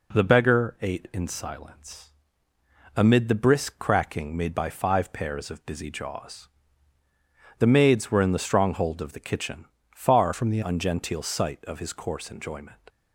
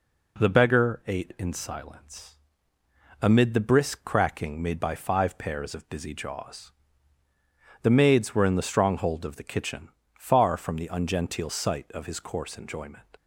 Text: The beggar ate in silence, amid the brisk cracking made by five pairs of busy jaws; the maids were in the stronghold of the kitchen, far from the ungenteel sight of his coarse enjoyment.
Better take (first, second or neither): second